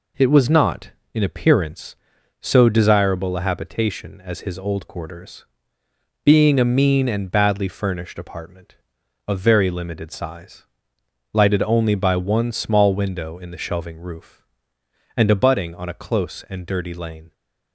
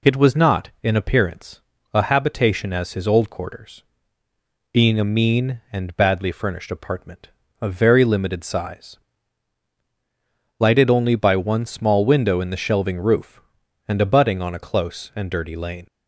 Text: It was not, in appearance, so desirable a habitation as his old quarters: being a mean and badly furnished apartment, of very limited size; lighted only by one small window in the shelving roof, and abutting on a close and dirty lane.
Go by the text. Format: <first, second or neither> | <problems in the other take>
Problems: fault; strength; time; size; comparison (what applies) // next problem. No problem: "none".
first | skips "so desirable"; at 1.7 s